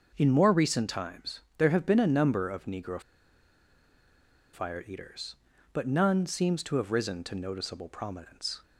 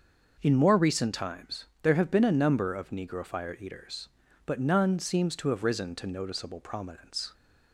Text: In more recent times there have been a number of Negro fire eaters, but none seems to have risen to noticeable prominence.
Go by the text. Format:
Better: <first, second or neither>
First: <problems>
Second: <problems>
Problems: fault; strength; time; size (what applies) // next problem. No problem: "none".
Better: second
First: starts louder than the rest; noticeable; until 1.1 s; 6 dB // pauses between "times" and "there"; slight; at 1.3 s; 0.18 s long // pauses between "Negro" and "fire"; strong; at 2.9 s; 1.5 s long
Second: starts louder than the rest; noticeable; until 1.4 s; 6 dB // pauses between "times" and "there"; slight; at 1.6 s; 0.18 s long